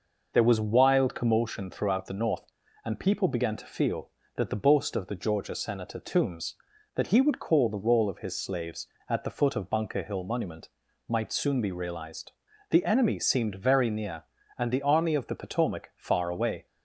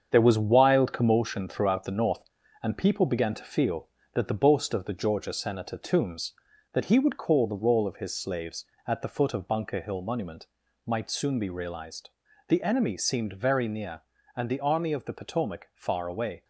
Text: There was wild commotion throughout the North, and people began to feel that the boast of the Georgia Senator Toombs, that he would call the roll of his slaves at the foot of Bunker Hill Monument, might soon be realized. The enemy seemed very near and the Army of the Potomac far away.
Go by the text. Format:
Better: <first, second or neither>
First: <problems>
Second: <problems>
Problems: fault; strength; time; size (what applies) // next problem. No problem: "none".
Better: first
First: none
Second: gets quieter; throughout; 6 dB